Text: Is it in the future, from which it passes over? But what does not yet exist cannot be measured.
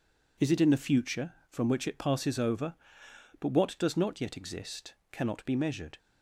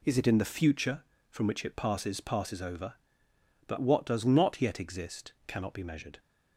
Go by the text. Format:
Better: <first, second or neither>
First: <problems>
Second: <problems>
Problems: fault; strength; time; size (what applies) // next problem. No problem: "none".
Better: first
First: pauses between "exist" and "cannot"; slight; at 4.9 s; 0.18 s long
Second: says "passes" twice; at 2.1 s // pauses between "exist" and "cannot"; slight; at 5.3 s; 0.16 s long